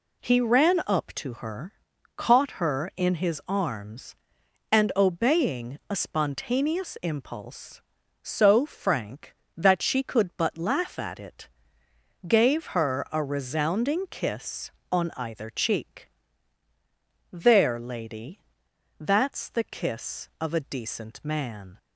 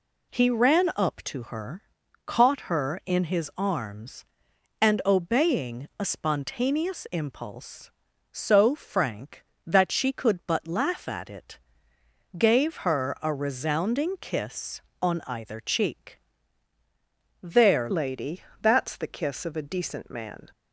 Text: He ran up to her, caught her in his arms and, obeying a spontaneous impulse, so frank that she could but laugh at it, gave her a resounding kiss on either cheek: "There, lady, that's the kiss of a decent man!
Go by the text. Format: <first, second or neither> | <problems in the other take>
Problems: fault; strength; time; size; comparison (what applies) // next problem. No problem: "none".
first | changes voice at "lady"; from 17.9 s on; 2.6 s long